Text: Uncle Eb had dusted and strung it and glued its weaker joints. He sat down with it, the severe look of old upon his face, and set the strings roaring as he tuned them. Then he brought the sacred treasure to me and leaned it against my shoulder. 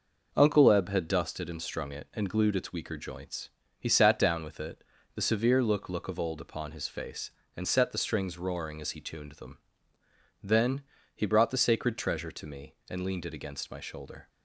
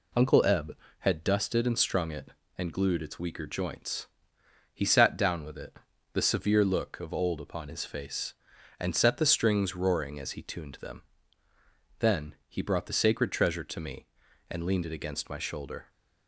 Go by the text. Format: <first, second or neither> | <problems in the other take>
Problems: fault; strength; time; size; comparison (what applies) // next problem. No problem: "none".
second | says "look" twice; at 5.8 s // pauses between "Then" and "he"; slight; at 10.8 s; 0.32 s long